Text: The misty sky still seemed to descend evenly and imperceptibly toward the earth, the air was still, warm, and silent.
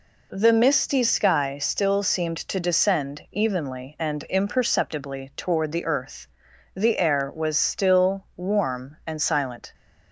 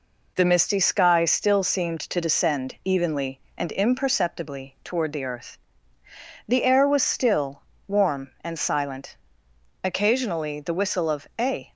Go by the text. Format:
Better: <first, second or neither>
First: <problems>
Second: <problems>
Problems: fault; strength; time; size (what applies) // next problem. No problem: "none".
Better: first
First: none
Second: goes on to say "Occasionally the whistle of a"; strong; from 9.8 s on; 1.8 s long